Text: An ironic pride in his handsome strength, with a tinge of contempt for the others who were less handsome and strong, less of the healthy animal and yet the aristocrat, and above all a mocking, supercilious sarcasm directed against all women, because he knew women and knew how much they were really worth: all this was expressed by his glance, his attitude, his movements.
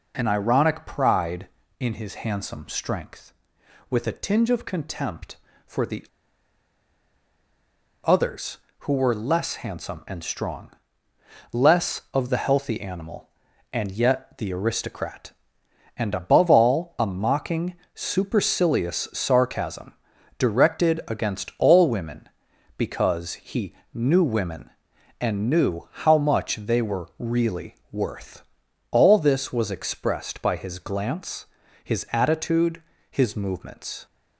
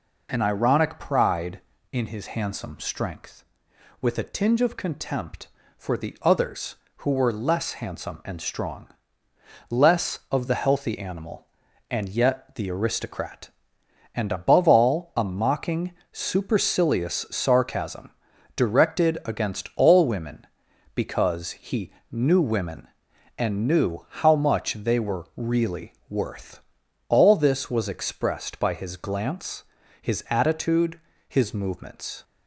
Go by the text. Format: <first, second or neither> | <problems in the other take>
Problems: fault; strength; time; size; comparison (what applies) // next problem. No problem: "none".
second | pauses between "the" and "others"; strong; at 6.0 s; 1.9 s long // pauses between "sarcasm" and "directed"; noticeable; at 19.9 s; 0.48 s long; noticeable in the second // pauses between "he" and "knew"; slight; at 23.7 s; 0.22 s long; slight in the second // pauses between "really" and "worth"; slight; at 27.7 s; 0.16 s long; slight in the second